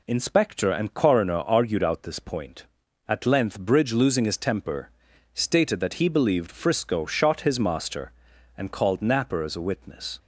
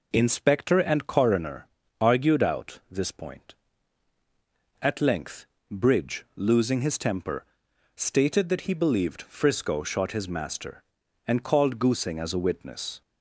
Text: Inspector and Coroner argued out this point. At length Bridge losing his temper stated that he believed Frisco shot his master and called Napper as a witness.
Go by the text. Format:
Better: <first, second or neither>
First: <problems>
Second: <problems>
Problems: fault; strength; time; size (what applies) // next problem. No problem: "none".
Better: first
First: pauses between "temper" and "stated"; at 4.8 s; 0.44 s long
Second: pauses between "Coroner" and "argued"; slight; at 1.6 s; 0.34 s long // pauses between "length" and "Bridge"; slight; at 5.4 s; 0.24 s long // pauses between "temper" and "stated"; noticeable; at 7.4 s; 0.50 s long // says "Goosing" for "Napper"; at 11.7 s